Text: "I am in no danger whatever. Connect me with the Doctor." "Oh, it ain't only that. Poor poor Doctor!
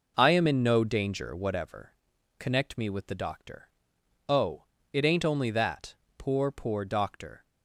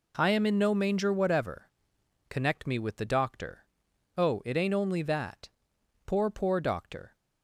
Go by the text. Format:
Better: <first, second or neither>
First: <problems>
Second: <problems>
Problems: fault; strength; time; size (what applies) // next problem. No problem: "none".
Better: first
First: none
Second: says "manger" for "danger"; at 0.7 s